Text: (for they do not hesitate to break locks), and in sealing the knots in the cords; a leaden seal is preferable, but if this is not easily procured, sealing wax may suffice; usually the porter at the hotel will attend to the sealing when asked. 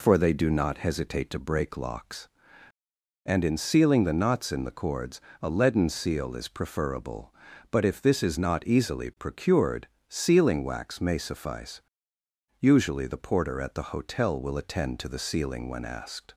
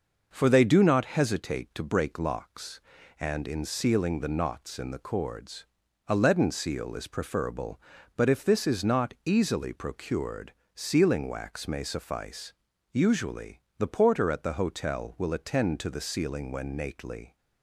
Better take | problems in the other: first | pauses between "usually" and "the"; slight; at 13.6 s; 0.18 s long // says "nately" for "asked"; at 16.7 s

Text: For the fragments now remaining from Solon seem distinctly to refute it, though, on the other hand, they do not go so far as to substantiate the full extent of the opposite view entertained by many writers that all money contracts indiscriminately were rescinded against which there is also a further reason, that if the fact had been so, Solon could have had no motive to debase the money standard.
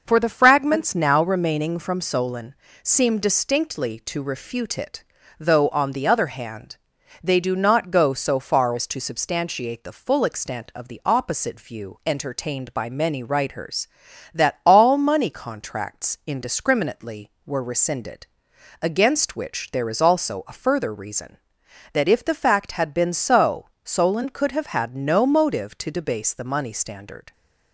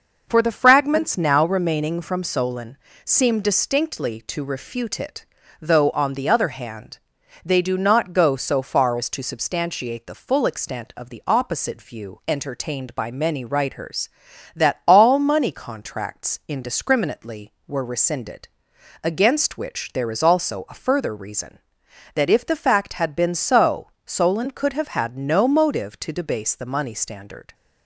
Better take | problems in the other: neither | pauses between "Solon" and "seem"; slight; the same in both // pauses between "rescinded" and "against"; noticeable; the same in both

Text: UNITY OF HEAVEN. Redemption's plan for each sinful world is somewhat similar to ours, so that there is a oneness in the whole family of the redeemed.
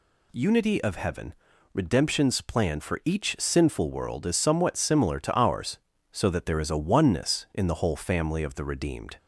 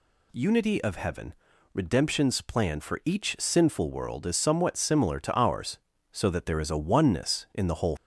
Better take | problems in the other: first | stops before "family of the redeemed"; at 7.9 s

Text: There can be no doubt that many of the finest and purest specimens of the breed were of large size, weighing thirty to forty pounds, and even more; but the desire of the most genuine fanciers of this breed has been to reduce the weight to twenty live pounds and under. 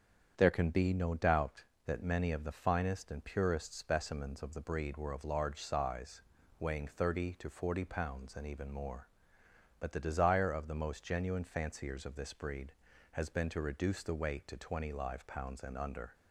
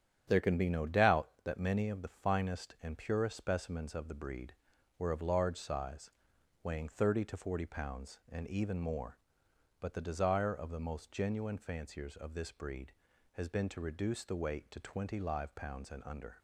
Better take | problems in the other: neither | starts louder than the rest; strong; the same in both

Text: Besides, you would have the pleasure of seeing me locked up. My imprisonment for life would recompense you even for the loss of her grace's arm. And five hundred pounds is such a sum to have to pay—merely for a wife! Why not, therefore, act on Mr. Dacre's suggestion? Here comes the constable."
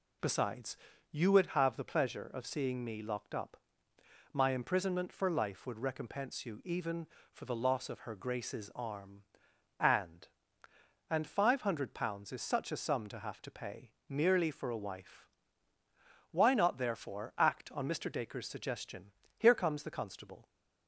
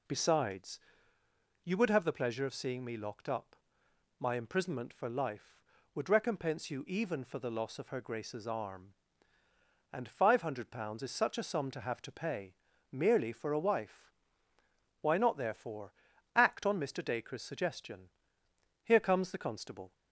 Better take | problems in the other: second | says "And" twice; at 11.0 s

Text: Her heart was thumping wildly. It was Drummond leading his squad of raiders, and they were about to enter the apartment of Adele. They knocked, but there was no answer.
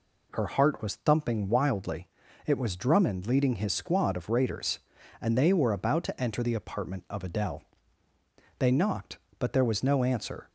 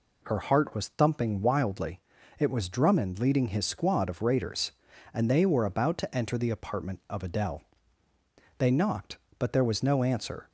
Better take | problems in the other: neither | none

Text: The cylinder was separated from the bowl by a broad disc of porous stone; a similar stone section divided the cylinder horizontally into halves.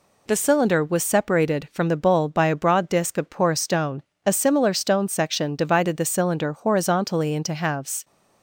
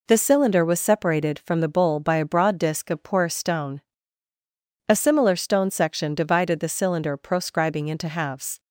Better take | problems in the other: first | says "proscribing" for "horizontally"; at 7.1 s

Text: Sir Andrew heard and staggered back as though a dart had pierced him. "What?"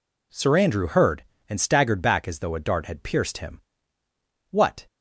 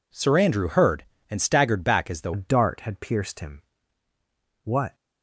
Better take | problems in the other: first | changes voice at "a"; from 2.3 s on; 2.6 s long

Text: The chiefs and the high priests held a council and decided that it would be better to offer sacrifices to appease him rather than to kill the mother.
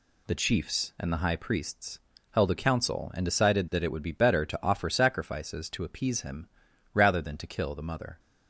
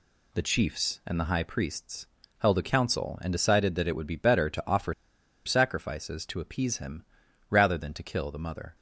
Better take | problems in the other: first | pauses between "priests" and "held"; slight; at 2.0 s; 0.32 s long; slight in the first // pauses between "offer" and "sacrifices"; noticeable; at 4.9 s; 0.52 s long // pauses between "him" and "rather"; at 7.0 s; 0.44 s long; also in the first

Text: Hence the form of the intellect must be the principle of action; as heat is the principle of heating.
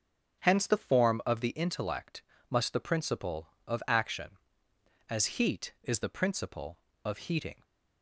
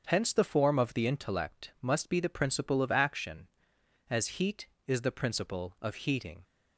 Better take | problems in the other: second | starts louder than the rest; until 1.4 s; 6.5 dB; strong in the second // pauses between "intellect" and "must"; slight; at 2.2 s; 0.26 s long // skips "be"; at 2.7 s

